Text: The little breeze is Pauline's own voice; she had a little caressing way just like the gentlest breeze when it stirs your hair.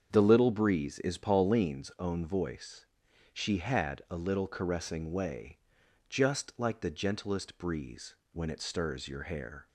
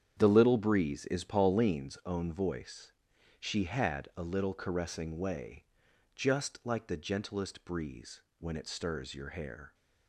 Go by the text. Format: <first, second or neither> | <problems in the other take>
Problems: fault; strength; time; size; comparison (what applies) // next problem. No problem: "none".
first | gets quieter; strong; throughout; 10.5 dB // starts louder than the rest; strong; until 1.1 s; 8.5 dB; strong in the first // pauses between "way" and "just"; noticeable; at 5.6 s; 0.50 s long; noticeable in the first // pauses between "breeze" and "when"; slight; at 8.2 s; 0.18 s long; slight in the first